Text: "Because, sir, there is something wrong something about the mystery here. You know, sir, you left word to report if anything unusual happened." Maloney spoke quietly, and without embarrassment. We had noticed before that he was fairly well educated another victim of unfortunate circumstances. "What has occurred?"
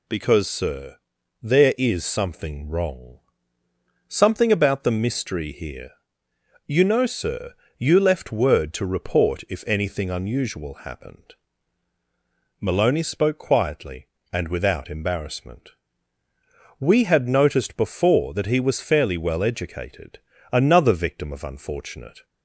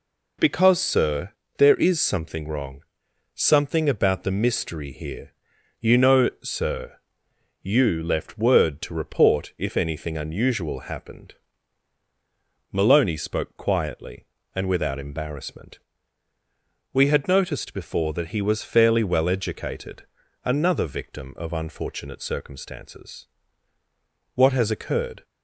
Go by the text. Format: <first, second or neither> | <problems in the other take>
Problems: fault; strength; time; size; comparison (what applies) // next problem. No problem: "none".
second | pauses between "wrong" and "something"; noticeable; at 3.1 s; 0.88 s long; noticeable in the second // pauses between "educated" and "another"; slight; at 20.1 s; 0.34 s long; also in the second // stops before "circumstances What has occurred"; at 22.2 s